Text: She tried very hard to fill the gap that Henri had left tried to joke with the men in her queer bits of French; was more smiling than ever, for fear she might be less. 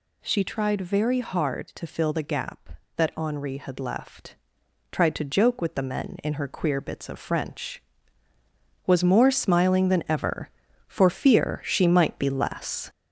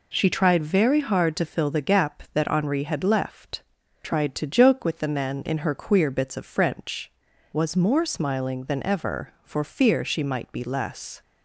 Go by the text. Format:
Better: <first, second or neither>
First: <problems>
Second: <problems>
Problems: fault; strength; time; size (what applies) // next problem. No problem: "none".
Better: second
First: gets louder; noticeable; throughout; 5.5 dB // pauses between "left" and "tried"; noticeable; at 4.3 s; 0.56 s long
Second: pauses between "left" and "tried"; at 3.6 s; 0.40 s long